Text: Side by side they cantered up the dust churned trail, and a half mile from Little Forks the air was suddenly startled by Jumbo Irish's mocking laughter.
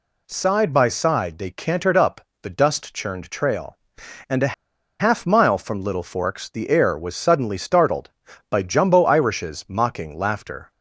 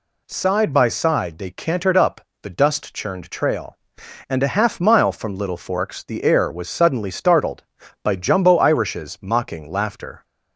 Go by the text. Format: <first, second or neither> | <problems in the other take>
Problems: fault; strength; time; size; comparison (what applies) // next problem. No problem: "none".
second | pauses between "up" and "the"; slight; at 2.1 s; 0.22 s long; slight in the second // pauses between "a" and "half"; noticeable; at 4.5 s; 0.47 s long